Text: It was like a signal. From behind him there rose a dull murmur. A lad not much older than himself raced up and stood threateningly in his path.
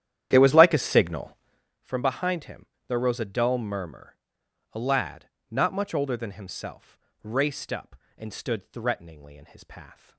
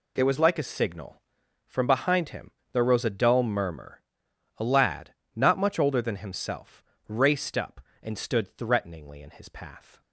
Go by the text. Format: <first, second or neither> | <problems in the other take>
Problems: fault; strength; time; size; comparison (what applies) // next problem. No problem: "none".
second | starts louder than the rest; strong; until 1.7 s; 11 dB // pauses between "him" and "there"; slight; at 2.6 s; 0.22 s long; slight in the second // pauses between "lad" and "not"; slight; at 5.2 s; 0.22 s long; slight in the second // pauses between "himself" and "raced"; slight; at 6.9 s; 0.24 s long; slight in the second